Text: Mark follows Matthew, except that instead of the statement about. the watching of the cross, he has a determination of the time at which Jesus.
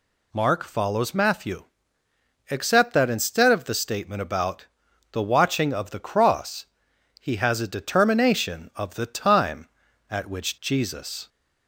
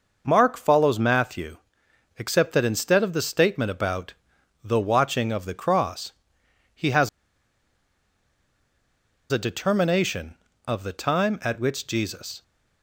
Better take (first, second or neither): first